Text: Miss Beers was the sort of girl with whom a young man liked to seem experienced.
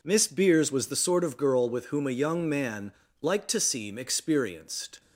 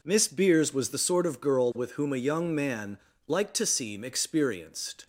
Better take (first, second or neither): neither